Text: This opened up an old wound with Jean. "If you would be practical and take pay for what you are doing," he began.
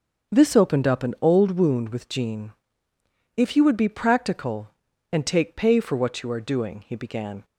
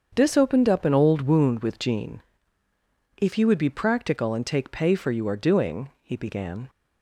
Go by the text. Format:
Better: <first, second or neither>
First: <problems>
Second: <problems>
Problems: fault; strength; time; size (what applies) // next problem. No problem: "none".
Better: first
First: starts louder than the rest; until 1.3 s; 6.5 dB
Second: starts louder than the rest; until 1.1 s; 7 dB // skips "what"; at 5.0 s